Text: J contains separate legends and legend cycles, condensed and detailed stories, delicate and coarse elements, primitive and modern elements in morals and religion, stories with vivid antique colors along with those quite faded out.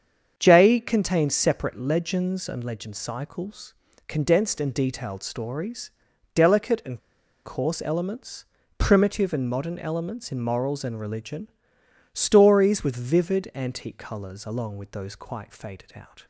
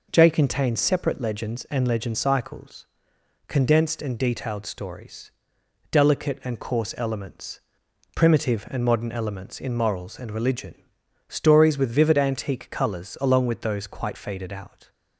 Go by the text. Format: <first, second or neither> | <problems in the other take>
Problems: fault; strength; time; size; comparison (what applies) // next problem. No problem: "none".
second | starts louder than the rest; strong; until 1.4 s; 7 dB // pauses between "and" and "coarse"; at 6.9 s; 0.45 s long